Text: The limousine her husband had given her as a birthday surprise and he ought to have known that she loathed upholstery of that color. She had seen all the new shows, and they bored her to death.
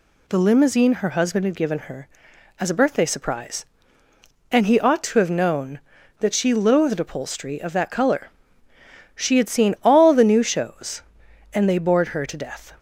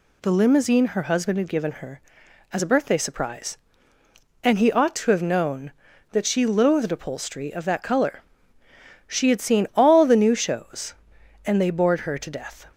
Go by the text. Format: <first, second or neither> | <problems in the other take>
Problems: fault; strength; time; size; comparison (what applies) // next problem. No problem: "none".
neither | none